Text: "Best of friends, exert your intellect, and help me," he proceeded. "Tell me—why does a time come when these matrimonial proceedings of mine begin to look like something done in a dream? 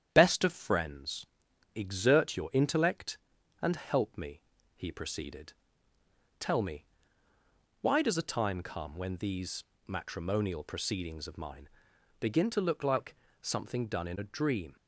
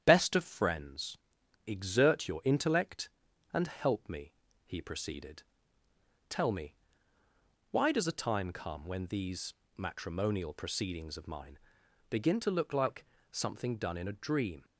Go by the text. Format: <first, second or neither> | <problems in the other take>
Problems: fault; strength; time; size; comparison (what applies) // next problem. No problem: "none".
neither | starts louder than the rest; strong; the same in both // pauses between "these" and "matrimonial"; slight; the same in both // pauses between "mine" and "begin"; noticeable; the same in both // pauses between "like" and "something"; slight; the same in both